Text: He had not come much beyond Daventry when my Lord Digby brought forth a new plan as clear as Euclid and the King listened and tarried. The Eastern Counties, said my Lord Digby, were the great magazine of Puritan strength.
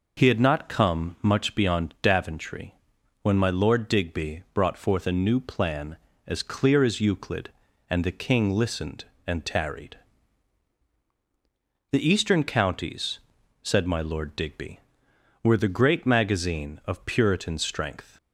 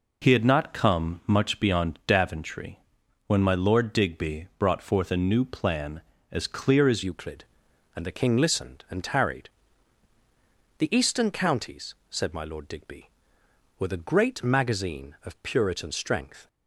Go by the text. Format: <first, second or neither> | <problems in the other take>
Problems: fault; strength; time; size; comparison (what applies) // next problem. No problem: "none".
first | pauses between "Daventry" and "when"; noticeable; at 2.7 s; 0.48 s long; noticeable in the first // changes voice at "Euclid"; from 7.0 s on; 9.4 s long